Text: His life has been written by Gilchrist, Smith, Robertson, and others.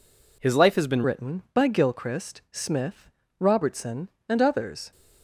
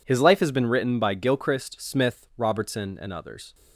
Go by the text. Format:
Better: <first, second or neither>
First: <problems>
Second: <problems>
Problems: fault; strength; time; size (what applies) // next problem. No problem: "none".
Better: second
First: changes voice at "written"; from 1.0 s on; 3.9 s long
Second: none